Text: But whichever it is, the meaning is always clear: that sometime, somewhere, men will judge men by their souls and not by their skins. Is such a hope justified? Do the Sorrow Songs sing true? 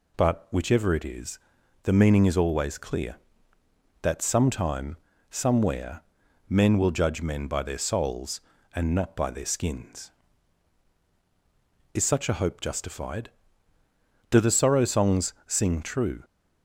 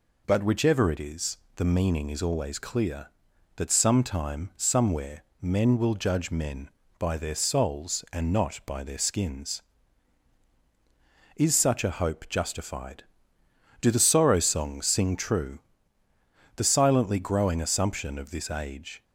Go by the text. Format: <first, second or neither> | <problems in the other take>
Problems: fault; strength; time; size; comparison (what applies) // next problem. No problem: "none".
first | goes on to say "The silently growing assumption of this age"; strong; from 16.5 s on; 2.4 s long